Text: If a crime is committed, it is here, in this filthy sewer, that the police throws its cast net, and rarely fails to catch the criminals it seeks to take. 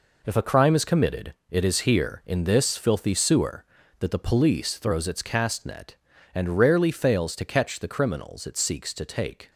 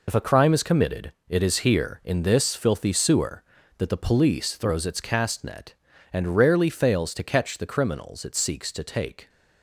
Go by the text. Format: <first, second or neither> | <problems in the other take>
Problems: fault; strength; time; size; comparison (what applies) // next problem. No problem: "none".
first | loses the start of "If"; at 0.0 s; 50 ms